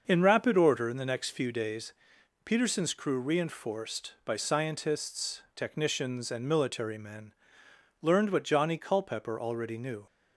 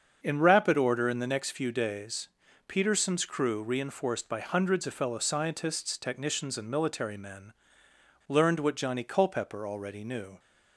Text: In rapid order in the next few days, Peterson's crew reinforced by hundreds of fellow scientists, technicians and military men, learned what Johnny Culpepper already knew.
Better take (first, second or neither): second